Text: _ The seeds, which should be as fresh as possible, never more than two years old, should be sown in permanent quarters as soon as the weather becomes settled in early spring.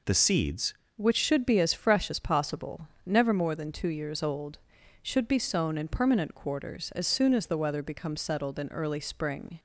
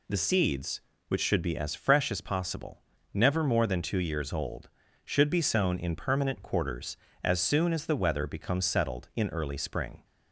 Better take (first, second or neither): second